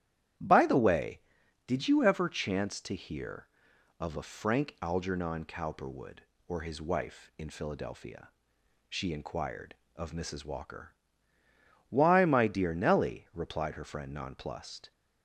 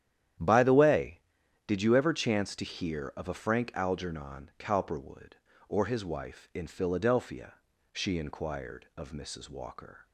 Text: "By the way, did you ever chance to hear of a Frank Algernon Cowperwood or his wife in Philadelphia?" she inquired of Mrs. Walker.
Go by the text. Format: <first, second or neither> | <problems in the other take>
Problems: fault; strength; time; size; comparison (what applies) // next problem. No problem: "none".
second | starts louder than the rest; strong; until 1.8 s; 11.5 dB; strong in the second // goes on to say "Why my dear Nellie replied her friend nonplussed"; strong; from 11.8 s on; 3.0 s long